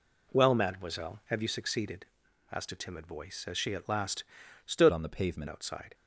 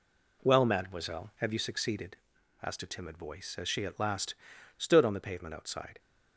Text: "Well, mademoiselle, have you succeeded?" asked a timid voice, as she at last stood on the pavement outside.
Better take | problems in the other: second | pauses between "last" and "stood"; at 4.2 s; 0.42 s long; also in the second // changes voice from "on" to "pavement"; from 4.8 to 5.4 s; 0.6 s long

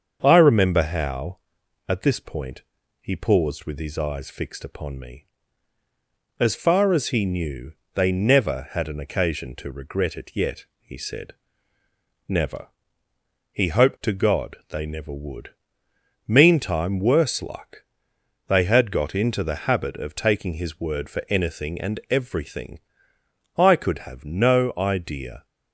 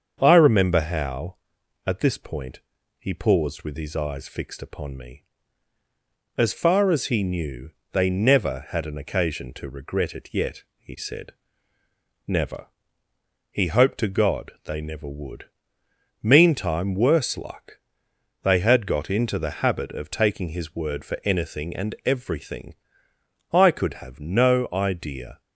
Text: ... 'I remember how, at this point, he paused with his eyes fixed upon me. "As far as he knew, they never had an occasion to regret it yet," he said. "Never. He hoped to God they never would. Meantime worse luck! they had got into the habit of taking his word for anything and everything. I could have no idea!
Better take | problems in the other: neither | starts louder than the rest; the same in both

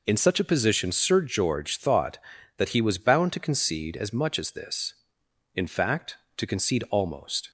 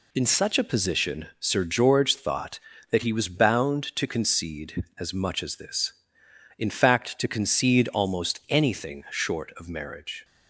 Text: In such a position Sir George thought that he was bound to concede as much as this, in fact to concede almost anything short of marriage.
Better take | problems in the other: second | stops before "anything short of marriage"; at 7.4 s

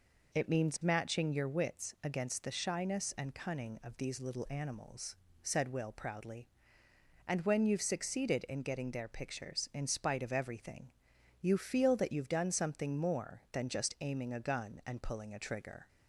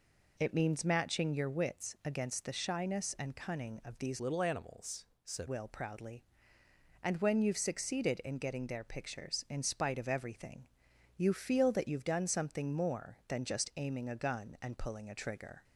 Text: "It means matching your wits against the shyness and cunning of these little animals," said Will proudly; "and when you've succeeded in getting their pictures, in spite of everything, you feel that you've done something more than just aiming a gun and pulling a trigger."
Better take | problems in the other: first | changes voice from "little" to "said"; from 4.1 to 5.4 s; 1.3 s long

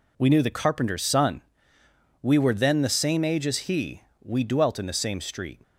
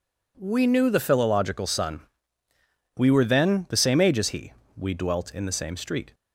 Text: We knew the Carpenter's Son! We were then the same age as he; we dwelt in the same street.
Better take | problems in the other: first | says "Philological" for "Carpenter's"; at 0.9 s

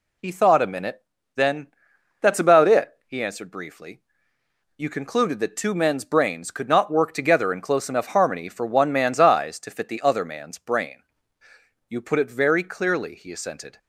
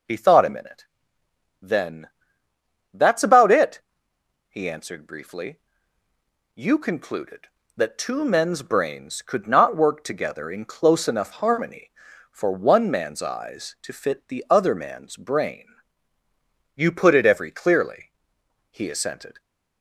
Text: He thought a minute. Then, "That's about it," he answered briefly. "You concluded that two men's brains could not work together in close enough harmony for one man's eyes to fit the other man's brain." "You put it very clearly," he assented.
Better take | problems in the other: first | says "every" for "very"; at 17.2 s

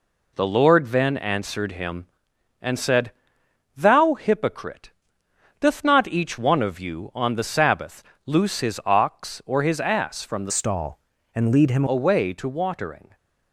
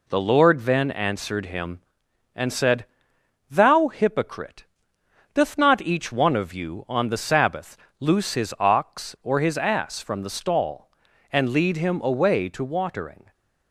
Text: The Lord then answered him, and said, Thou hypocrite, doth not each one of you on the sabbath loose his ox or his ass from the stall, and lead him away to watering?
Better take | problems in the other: second | pauses between "sabbath" and "loose"; slight; at 8.0 s; 0.22 s long; slight in the second // changes voice from "stall" to "him"; from 10.4 to 11.8 s; 1.4 s long

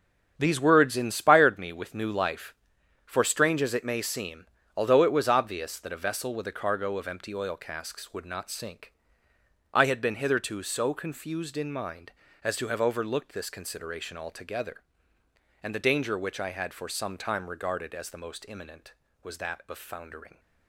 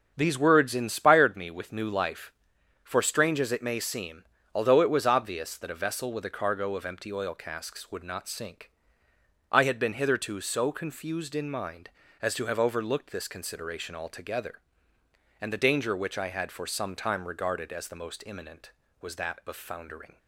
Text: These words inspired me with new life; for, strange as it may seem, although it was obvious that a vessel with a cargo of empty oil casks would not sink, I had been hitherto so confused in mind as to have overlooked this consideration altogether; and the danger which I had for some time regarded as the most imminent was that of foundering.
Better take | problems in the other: second | gets quieter; strong; throughout; 9.5 dB // starts louder than the rest; strong; until 1.3 s; 7.5 dB; also in the second

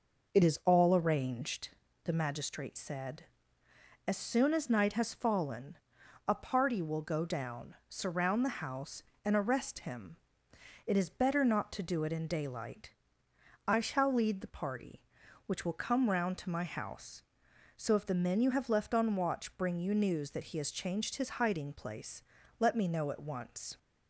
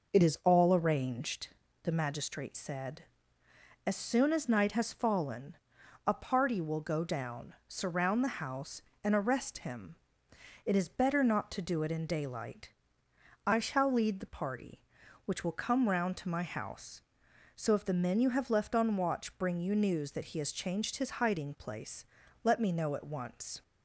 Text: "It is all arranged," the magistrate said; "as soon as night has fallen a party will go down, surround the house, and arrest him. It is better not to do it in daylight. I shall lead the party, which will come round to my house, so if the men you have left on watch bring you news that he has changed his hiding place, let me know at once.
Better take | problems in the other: neither | pauses between "fallen" and "a"; noticeable; the same in both

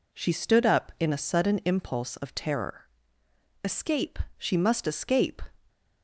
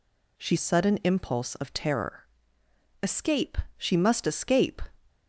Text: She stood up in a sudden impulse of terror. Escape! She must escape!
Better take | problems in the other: first | skips "stood up in a"; at 0.5 s

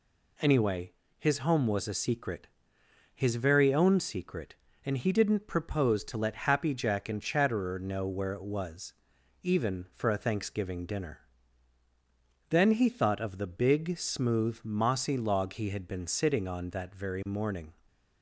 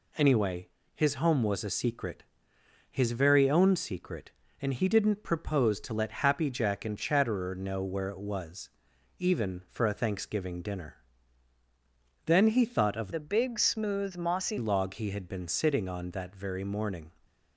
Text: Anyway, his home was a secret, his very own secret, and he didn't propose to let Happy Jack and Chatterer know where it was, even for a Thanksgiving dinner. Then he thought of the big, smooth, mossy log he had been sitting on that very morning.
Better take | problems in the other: first | changes voice from "the" to "mossy"; from 13.1 to 14.5 s; 1.4 s long

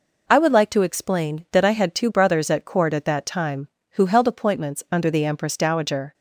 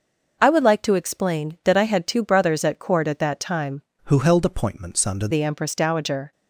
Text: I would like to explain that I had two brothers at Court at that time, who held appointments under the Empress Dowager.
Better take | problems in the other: first | changes voice from "who" to "under"; from 4.0 to 5.2 s; 1.2 s long

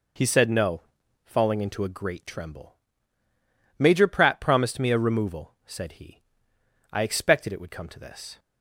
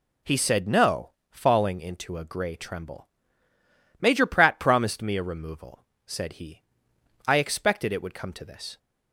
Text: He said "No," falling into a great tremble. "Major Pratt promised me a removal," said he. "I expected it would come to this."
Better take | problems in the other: first | says "grey" for "great"; at 2.2 s

